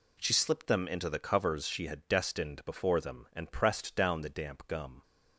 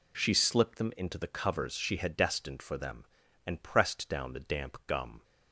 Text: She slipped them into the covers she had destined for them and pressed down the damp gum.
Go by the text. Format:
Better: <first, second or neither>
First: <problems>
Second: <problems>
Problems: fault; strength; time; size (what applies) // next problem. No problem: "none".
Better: second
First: says "before" for "for"; at 2.6 s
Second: none